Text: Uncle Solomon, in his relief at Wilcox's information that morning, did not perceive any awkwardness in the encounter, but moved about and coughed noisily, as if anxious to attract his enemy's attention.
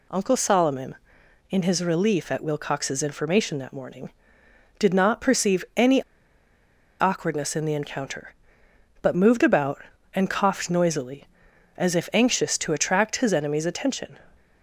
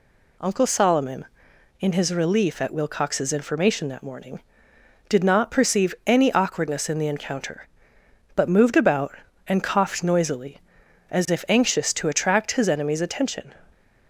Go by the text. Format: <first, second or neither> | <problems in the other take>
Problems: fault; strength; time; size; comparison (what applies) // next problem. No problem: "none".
second | pauses between "any" and "awkwardness"; noticeable; at 6.0 s; 0.97 s long